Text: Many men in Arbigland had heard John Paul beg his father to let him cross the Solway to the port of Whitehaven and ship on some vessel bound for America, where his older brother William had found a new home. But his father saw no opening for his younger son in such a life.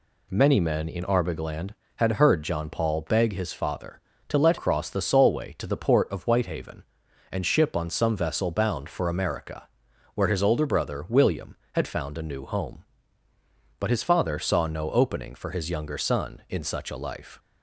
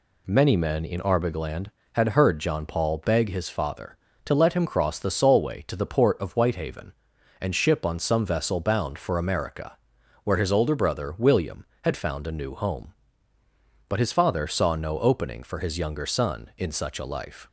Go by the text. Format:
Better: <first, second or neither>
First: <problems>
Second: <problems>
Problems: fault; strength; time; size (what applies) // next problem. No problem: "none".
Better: second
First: skips "him"; at 4.5 s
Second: none